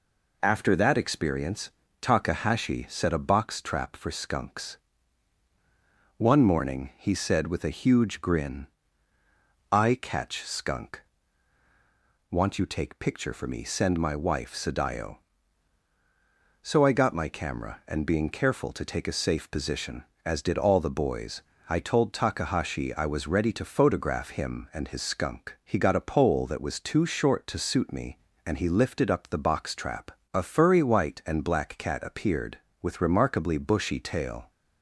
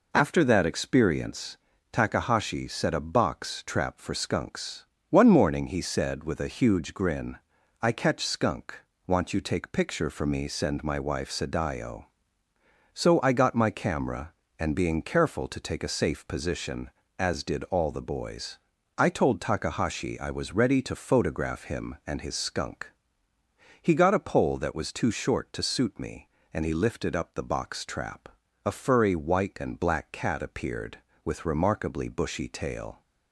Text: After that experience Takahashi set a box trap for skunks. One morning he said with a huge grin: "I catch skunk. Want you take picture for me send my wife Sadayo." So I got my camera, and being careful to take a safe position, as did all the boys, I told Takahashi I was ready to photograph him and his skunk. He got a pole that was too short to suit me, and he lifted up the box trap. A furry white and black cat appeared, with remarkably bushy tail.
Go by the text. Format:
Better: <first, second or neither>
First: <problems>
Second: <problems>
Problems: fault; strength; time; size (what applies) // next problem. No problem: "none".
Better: neither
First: pauses between "experience" and "Takahashi"; slight; at 1.6 s; 0.30 s long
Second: pauses between "experience" and "Takahashi"; at 1.5 s; 0.38 s long